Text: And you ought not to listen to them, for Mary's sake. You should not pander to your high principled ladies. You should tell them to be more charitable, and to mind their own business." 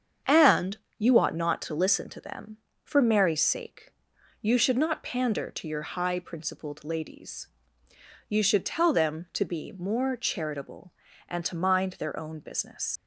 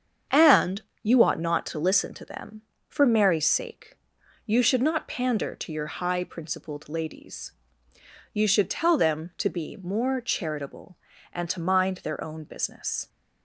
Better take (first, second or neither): second